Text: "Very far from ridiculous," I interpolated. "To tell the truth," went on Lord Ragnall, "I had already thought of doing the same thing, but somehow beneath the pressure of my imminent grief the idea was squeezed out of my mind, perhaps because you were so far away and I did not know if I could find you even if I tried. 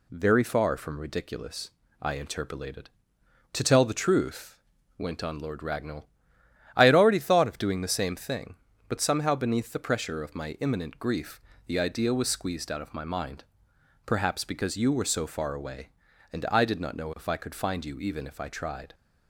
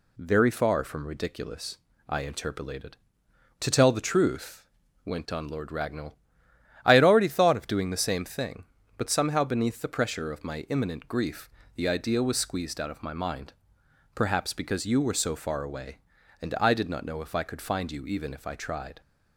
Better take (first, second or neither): neither